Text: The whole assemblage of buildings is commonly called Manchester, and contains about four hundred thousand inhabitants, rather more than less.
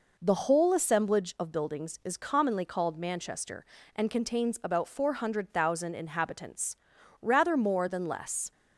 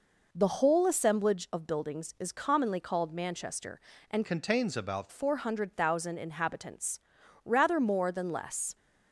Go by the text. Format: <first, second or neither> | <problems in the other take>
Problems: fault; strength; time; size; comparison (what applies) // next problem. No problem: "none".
first | changes voice from "contains" to "about"; from 4.2 to 5.1 s; 0.9 s long